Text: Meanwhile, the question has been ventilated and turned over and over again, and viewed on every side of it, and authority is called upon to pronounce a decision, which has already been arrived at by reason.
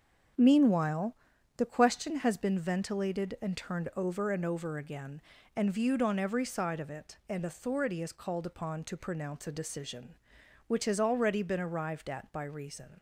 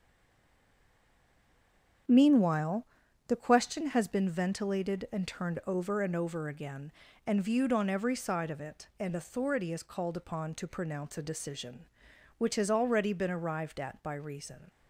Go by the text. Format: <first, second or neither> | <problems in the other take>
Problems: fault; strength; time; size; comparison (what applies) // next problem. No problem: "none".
first | stays silent before the first word; noticeable; until 2.0 s; 2.0 s long // starts louder than the rest; noticeable; until 3.4 s; 6 dB; noticeable in the first